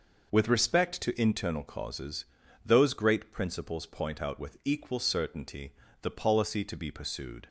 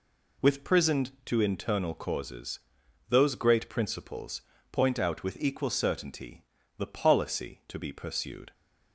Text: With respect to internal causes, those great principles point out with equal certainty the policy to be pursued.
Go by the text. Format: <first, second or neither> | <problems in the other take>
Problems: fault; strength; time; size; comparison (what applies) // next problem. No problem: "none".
first | says "prisoned" for "respect"; at 0.6 s // pauses between "principles" and "point"; slight; at 4.4 s; 0.28 s long // pauses between "certainty" and "the"; slight; at 6.4 s; 0.34 s long; slight in the first